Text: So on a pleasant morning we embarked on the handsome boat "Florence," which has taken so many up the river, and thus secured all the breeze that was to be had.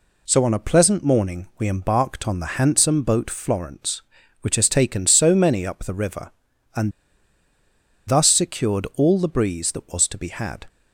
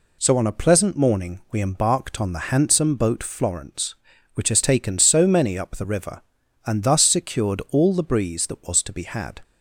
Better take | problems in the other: second | pauses between "and" and "thus"; at 6.9 s; 1.1 s long

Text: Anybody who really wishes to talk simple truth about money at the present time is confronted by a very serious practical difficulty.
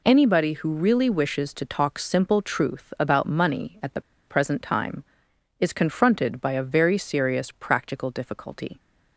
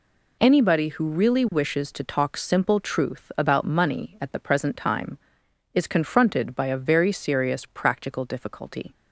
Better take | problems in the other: second | pauses between "the" and "present"; slight; at 4.0 s; 0.26 s long

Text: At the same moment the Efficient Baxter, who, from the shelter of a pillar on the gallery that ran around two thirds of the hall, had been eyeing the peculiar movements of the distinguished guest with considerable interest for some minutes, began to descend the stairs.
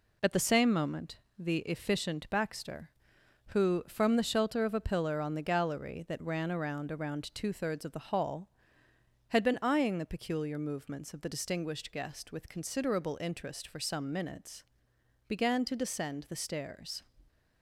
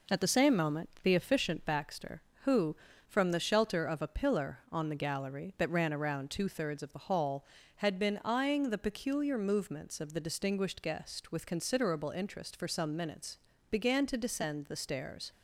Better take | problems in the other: second | pauses between "moment" and "the"; slight; at 1.1 s; 0.18 s long // says "around" twice; at 6.9 s

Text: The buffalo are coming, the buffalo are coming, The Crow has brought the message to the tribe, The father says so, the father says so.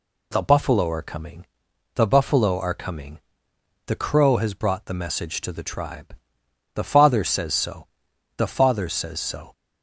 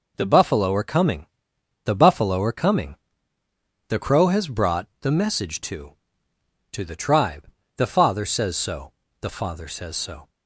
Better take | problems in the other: first | says "to" twice; at 6.7 s

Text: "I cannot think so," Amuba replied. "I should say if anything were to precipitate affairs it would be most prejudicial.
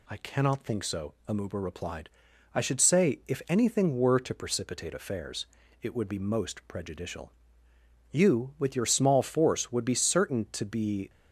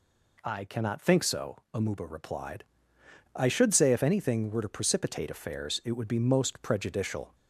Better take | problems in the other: second | pauses between "affairs" and "it"; slight; at 5.4 s; 0.36 s long // goes on to say "You with your small force would be certain to be"; strong; from 8.0 s on; 3.0 s long

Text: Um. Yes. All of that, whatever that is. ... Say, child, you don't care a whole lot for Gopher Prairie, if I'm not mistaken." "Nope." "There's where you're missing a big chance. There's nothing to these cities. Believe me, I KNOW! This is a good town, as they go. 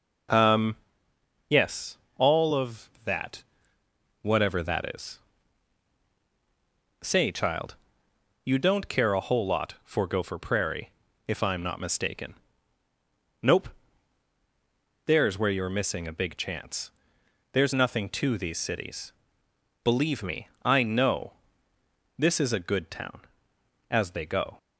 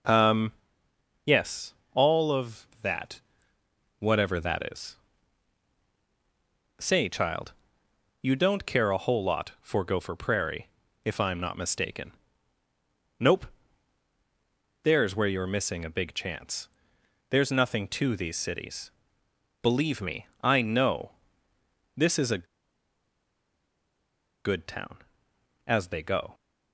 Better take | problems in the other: first | pauses between "a" and "good"; strong; at 22.4 s; 1.9 s long

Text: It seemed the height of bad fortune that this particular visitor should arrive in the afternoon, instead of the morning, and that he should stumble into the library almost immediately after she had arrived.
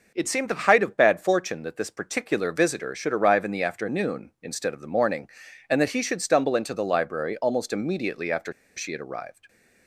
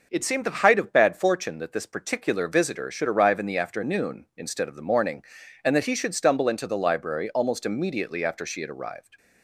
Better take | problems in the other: second | pauses between "after" and "she"; slight; at 8.5 s; 0.24 s long

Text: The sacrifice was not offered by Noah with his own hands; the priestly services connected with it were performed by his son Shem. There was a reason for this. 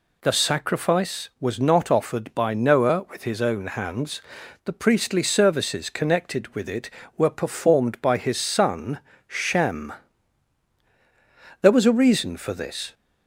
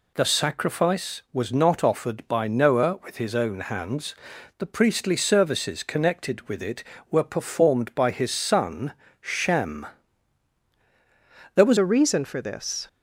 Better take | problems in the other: first | pauses between "son" and "Shem"; slight; at 8.9 s; 0.28 s long; slight in the first // changes voice at "a"; from 11.7 s on; 1.1 s long

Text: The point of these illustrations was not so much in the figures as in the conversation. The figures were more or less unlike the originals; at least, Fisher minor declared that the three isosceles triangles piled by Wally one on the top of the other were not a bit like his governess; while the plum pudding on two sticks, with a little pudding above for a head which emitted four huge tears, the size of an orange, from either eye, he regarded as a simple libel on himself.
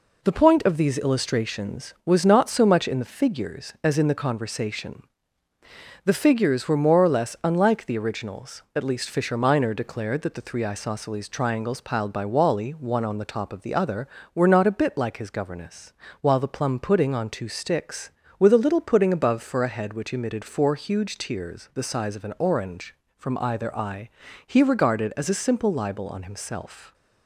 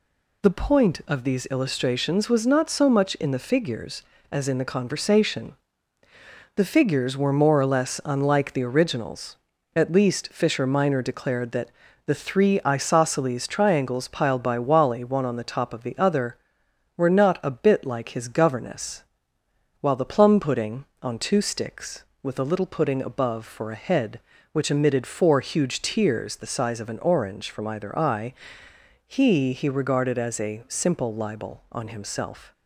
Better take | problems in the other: first | pauses between "that" and "the"; slight; at 11.6 s; 0.36 s long // says "he" twice; at 29.5 s

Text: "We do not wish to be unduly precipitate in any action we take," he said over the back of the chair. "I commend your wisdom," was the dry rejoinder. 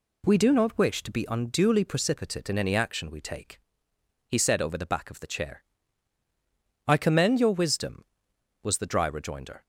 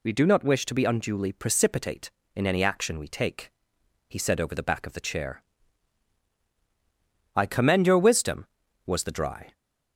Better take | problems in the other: first | stops before "rejoinder"; at 9.5 s

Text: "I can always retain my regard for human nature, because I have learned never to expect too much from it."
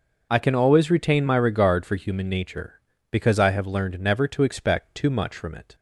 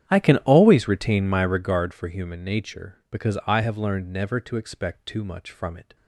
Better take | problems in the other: first | starts louder than the rest; strong; until 1.7 s; 10 dB

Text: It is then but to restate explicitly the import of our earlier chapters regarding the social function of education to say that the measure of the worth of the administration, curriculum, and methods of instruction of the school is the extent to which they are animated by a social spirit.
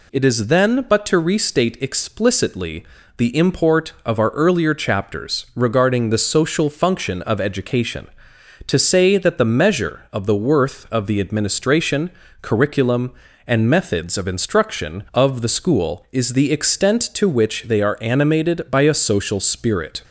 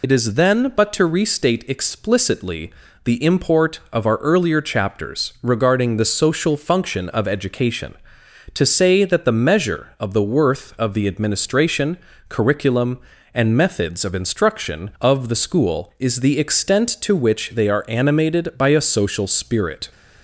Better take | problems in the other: first | loses the start of "It"; at 0.0 s; 55 ms // pauses between "explicitly" and "the"; slight; at 2.7 s; 0.34 s long; slight in the first

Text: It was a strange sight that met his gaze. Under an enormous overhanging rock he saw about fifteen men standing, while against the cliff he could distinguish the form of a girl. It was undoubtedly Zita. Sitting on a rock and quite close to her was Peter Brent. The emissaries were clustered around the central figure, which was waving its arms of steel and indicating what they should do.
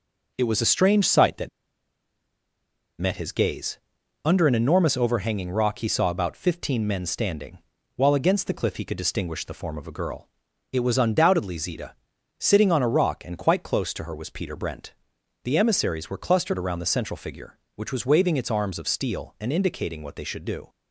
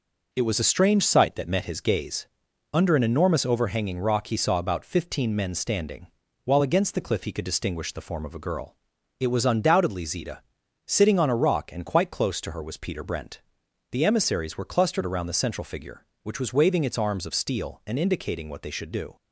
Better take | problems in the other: second | pauses between "that" and "met"; strong; at 1.4 s; 1.5 s long

